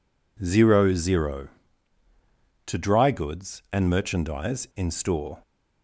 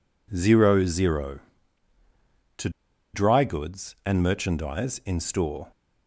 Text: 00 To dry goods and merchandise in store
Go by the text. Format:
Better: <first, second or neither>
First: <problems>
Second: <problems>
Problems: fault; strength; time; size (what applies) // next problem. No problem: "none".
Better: first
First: none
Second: pauses between "To" and "dry"; at 2.6 s; 0.44 s long